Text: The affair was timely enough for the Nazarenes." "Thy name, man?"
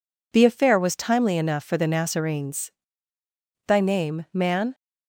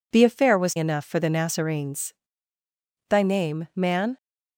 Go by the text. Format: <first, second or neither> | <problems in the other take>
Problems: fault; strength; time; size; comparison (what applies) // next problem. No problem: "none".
first | skips "timely"; at 0.7 s